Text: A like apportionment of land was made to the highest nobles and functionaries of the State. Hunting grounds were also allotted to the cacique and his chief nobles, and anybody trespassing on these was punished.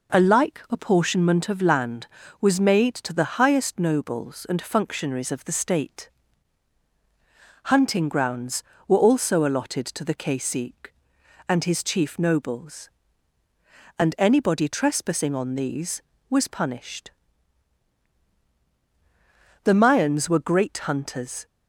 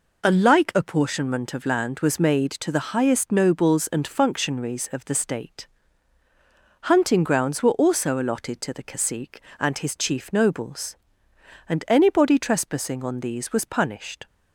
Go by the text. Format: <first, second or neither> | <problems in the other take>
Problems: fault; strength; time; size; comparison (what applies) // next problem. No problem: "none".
second | goes on to say "The Mayans were great hunters"; strong; from 19.6 s on; 1.8 s long